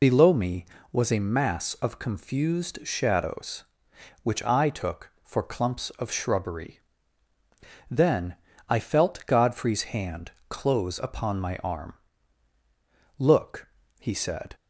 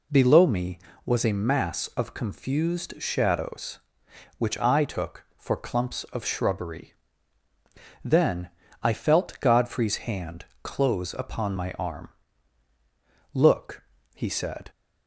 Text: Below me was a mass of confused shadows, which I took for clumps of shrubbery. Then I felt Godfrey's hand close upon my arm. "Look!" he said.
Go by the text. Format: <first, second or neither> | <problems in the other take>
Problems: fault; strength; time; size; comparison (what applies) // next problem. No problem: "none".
second | loses the start of "Below"; at 0.0 s; 45 ms // pauses between "Then" and "I"; slight; at 8.3 s; 0.34 s long; slight in the second // pauses between "hand" and "close"; slight; at 10.3 s; 0.16 s long; slight in the second